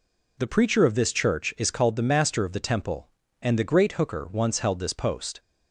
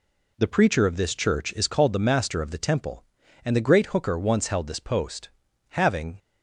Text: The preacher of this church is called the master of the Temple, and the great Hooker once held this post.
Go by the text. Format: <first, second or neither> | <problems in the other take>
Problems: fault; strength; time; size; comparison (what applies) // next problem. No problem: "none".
first | goes on to say "Having"; slight; from 5.7 s on; 0.48 s long